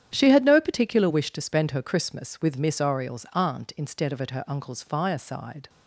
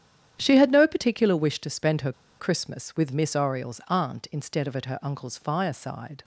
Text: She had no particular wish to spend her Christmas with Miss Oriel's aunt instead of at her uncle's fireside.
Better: first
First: starts louder than the rest; strong; until 1.1 s; 9.5 dB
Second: starts louder than the rest; strong; until 1.3 s; 10 dB // pauses between "her" and "Christmas"; slight; at 2.1 s; 0.26 s long

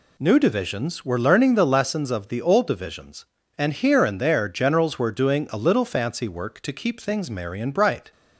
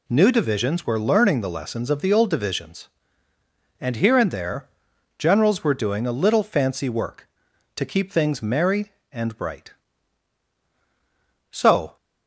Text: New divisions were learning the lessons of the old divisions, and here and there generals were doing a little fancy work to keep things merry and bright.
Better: first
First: none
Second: pauses between "there" and "generals"; noticeable; at 4.6 s; 0.50 s long // goes on to say "So"; slight; from 11.5 s on; 0.46 s long

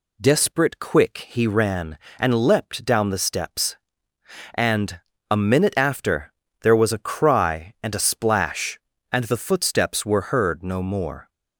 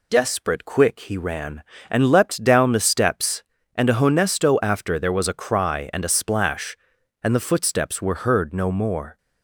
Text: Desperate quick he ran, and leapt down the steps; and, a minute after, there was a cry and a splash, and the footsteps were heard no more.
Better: first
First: none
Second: says "honesto" for "minute"; at 3.9 s

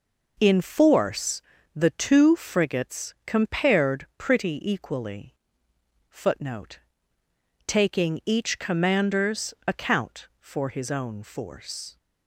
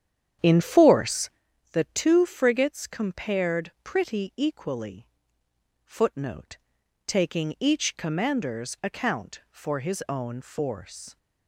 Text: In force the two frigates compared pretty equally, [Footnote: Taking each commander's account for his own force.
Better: first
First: pauses between "force" and "the"; slight; at 1.4 s; 0.32 s long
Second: starts louder than the rest; strong; until 1.5 s; 9.5 dB // pauses between "force" and "the"; at 1.2 s; 0.44 s long

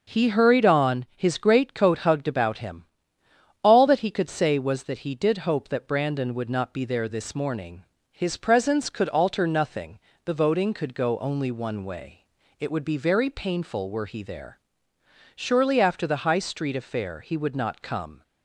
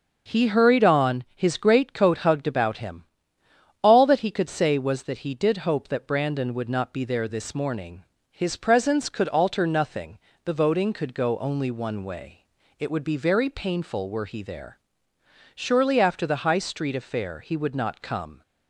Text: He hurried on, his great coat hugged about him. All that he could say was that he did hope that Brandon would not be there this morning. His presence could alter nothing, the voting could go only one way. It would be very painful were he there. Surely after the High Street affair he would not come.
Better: neither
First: starts louder than the rest; until 1.2 s; 6.5 dB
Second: starts louder than the rest; until 1.4 s; 6.5 dB

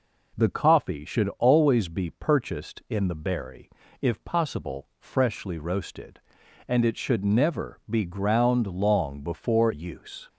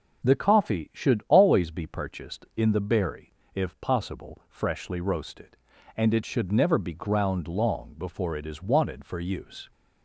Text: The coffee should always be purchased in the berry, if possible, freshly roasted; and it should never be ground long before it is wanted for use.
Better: second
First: skips "it is wanted for"; at 9.7 s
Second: none

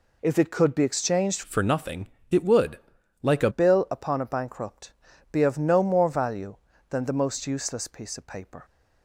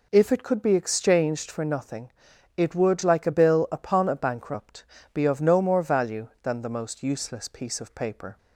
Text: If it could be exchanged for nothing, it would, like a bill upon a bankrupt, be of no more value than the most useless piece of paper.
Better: second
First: changes voice from "for" to "a"; from 1.4 to 3.4 s; 2.0 s long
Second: none

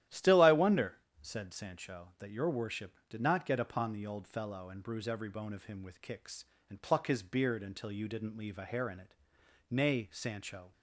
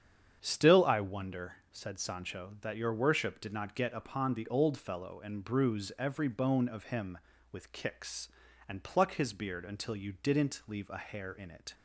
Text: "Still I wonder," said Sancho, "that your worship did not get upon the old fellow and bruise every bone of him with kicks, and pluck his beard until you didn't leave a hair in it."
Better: second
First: starts louder than the rest; strong; until 1.2 s; 12 dB // goes on to say "Nay Sancho"; noticeable; from 9.7 s on; 1.0 s long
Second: starts louder than the rest; strong; until 1.4 s; 8 dB

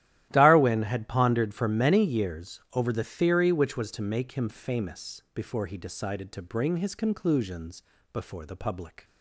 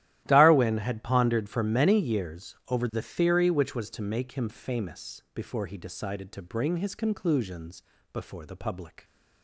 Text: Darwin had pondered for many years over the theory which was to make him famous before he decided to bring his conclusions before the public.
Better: neither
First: starts louder than the rest; strong; until 1.3 s; 13 dB // pauses between "conclusions" and "before"; slight; at 7.8 s; 0.30 s long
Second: starts louder than the rest; strong; until 1.2 s; 13.5 dB // pauses between "conclusions" and "before"; slight; at 7.8 s; 0.30 s long

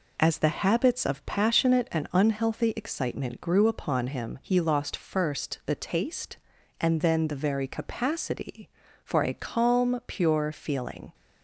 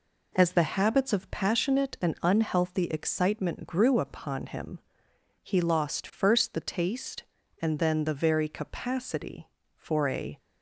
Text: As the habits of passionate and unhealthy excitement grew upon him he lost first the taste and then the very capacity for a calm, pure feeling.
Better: first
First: none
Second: pauses between "him" and "he"; noticeable; at 4.7 s; 0.64 s long // stops before "calm pure feeling"; at 10.3 s

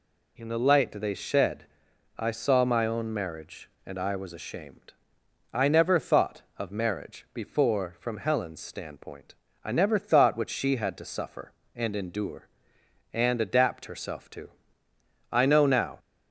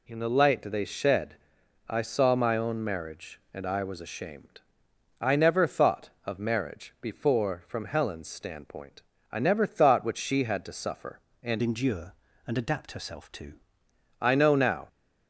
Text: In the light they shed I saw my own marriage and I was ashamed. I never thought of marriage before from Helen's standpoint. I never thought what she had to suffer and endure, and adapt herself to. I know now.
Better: first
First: pauses between "shed" and "I"; noticeable; at 1.6 s; 0.52 s long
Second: pauses between "shed" and "I"; noticeable; at 1.3 s; 0.52 s long // changes voice from "endure" to "to"; from 11.6 to 13.5 s; 1.9 s long

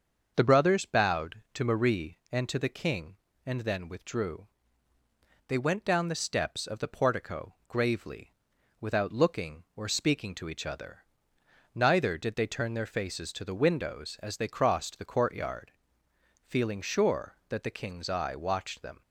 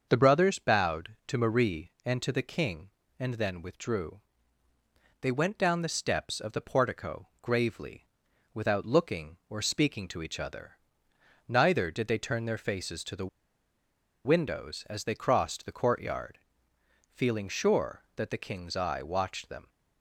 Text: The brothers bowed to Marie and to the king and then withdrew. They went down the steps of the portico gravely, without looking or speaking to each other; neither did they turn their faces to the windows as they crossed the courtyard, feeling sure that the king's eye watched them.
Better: first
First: starts louder than the rest; until 1.3 s; 6.5 dB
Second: starts louder than the rest; until 1.0 s; 6.5 dB // pauses between "the" and "windows"; noticeable; at 13.2 s; 0.98 s long

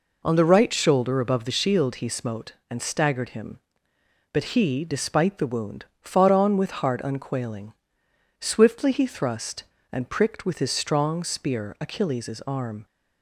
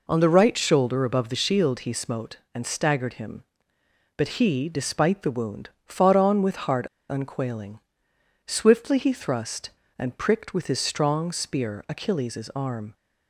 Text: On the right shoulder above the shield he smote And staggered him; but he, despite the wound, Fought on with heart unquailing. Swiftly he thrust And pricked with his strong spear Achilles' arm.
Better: first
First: none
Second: pauses between "heart" and "unquailing"; slight; at 6.8 s; 0.22 s long

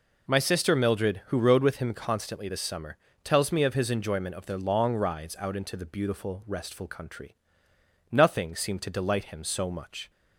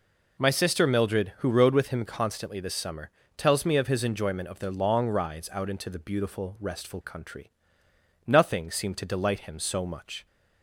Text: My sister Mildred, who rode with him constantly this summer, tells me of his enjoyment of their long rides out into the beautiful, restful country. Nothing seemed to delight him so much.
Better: neither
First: none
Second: none

